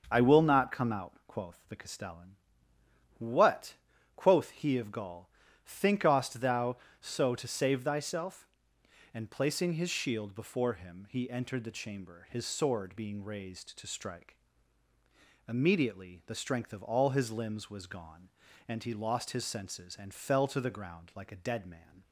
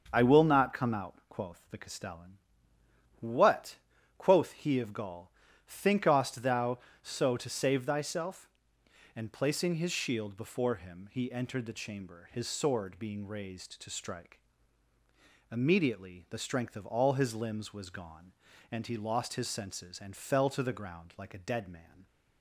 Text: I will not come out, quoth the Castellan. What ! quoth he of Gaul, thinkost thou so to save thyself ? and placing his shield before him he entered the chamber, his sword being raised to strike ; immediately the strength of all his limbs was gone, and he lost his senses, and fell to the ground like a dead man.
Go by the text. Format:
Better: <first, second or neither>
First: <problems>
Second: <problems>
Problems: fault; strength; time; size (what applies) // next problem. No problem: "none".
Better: neither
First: starts louder than the rest; until 1.1 s; 6.5 dB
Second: starts louder than the rest; until 1.1 s; 6.5 dB